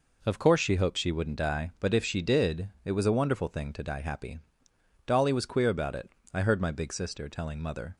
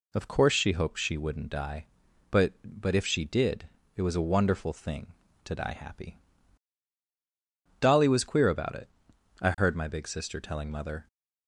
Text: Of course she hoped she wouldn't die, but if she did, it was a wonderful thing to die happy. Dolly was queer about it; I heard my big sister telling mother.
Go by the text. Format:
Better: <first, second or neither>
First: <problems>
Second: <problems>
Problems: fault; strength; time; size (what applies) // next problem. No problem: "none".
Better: first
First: none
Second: says "but" twice; at 2.6 s